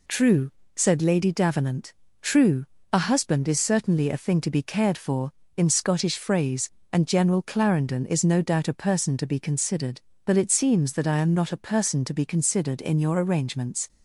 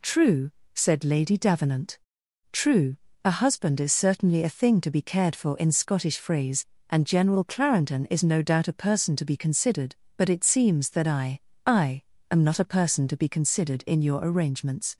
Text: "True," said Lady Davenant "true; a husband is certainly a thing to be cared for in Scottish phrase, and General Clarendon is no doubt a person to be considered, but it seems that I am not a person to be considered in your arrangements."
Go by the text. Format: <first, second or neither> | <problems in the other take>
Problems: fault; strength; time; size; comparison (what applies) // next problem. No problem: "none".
first | pauses between "Davenant" and "true"; noticeable; at 1.9 s; 0.54 s long; slight in the first // says "I" twice; at 11.6 s